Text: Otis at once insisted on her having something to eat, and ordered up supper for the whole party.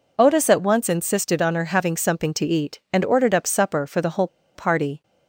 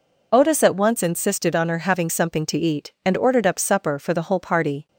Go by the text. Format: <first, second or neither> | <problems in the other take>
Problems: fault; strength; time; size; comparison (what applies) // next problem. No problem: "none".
second | pauses between "whole" and "party"; slight; at 4.2 s; 0.28 s long